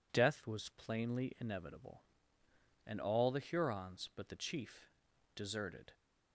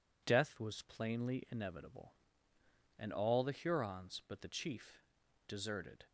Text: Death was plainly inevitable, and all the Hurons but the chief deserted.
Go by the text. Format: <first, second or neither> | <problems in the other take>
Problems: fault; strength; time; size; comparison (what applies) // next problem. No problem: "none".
neither | pauses between "chief" and "deserted"; noticeable; the same in both